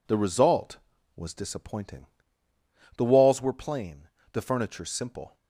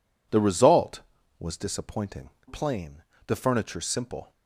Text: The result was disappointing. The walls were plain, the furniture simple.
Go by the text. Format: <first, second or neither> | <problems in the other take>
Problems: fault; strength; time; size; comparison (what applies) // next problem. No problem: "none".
first | skips "The walls were"; at 2.3 s